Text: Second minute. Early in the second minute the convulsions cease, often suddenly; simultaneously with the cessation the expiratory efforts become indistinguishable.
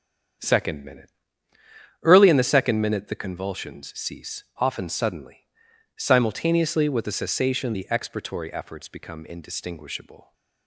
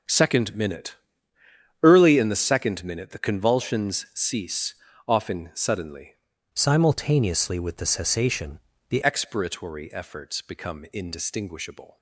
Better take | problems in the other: first | starts louder than the rest; until 1.9 s; 6.5 dB; strong in the first // changes voice from "simultaneously" to "the"; from 6.5 to 9.0 s; 2.5 s long // pauses between "cessation" and "the"; slight; at 8.5 s; 0.30 s long

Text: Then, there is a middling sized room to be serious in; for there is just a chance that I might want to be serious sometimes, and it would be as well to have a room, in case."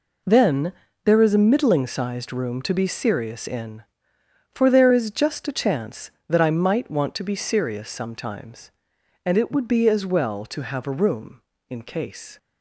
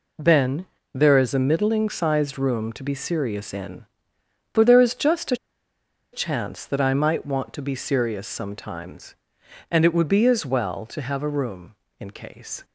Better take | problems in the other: first | pauses between "a" and "chance"; noticeable; at 5.3 s; 0.77 s long

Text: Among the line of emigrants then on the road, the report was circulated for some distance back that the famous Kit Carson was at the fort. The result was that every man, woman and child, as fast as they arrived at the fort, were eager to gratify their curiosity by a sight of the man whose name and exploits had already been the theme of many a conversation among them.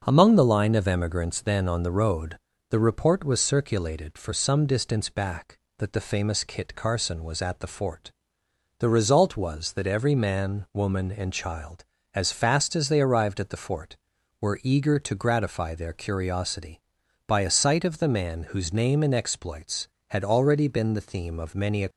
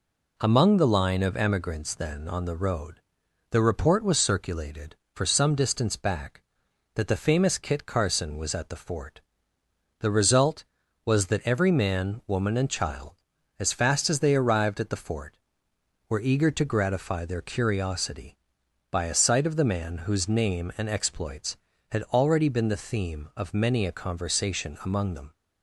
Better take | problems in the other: second | starts louder than the rest; noticeable; until 1.0 s; 6 dB // stops before "conversation among them"; at 21.8 s

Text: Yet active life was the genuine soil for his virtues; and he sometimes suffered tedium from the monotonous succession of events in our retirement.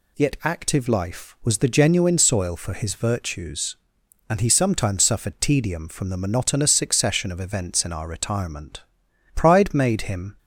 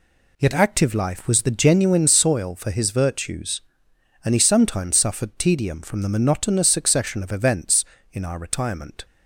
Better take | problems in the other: second | goes on to say "Pride made him"; noticeable; from 9.3 s on; 1.0 s long

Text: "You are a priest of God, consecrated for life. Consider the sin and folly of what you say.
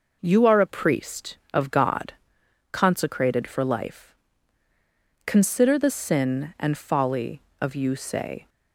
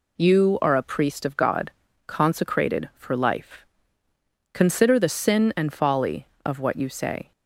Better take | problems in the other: second | skips "what"; at 7.7 s

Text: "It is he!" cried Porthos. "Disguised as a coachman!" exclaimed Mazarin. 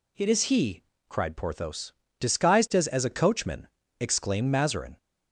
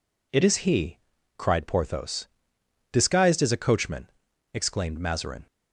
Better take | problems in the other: second | says "as" twice; at 2.8 s

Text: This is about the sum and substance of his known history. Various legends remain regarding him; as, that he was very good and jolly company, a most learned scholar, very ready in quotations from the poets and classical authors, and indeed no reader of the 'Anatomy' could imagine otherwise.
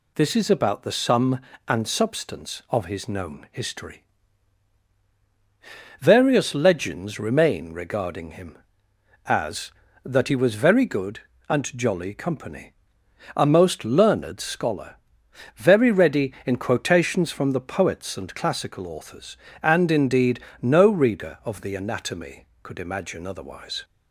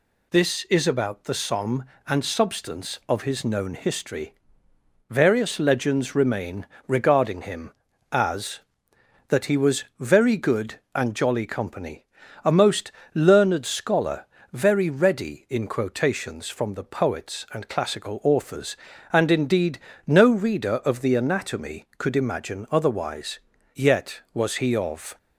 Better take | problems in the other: first | pauses between "remain" and "regarding"; slight; at 6.6 s; 0.18 s long // pauses between "was" and "very"; slight; at 9.8 s; 0.16 s long // pauses between "most" and "learned"; slight; at 12.9 s; 0.24 s long // pauses between "indeed" and "no"; slight; at 19.7 s; 0.26 s long; slight in the first // goes on to say "Yet was he of"; from 23.7 s on; 1.4 s long

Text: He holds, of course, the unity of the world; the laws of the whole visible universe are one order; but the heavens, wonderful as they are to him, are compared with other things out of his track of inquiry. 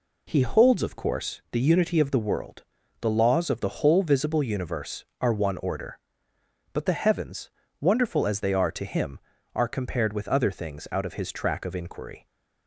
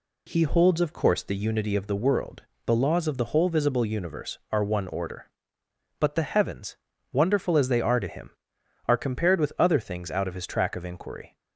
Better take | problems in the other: neither | none

